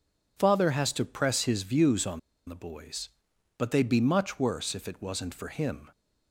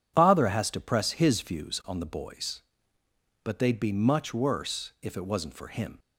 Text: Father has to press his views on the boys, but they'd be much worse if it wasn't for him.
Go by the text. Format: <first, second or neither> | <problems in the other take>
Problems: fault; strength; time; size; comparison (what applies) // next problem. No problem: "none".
second | pauses between "on" and "the"; slight; at 2.1 s; 0.27 s long